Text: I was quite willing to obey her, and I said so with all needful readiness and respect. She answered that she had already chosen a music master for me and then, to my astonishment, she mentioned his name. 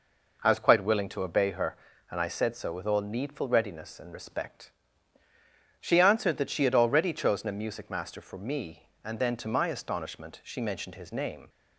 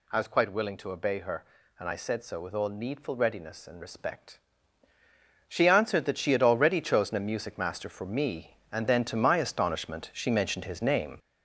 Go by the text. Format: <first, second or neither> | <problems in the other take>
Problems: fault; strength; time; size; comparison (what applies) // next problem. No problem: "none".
first | gets louder; noticeable; throughout; 6 dB